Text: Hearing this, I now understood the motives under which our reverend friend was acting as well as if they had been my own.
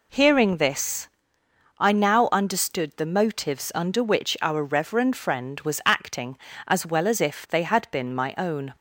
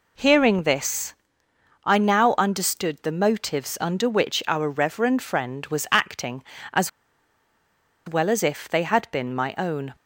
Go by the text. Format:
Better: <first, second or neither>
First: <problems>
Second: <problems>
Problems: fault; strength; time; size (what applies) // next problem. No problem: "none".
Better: first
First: none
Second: pauses between "as" and "well"; at 6.8 s; 1.1 s long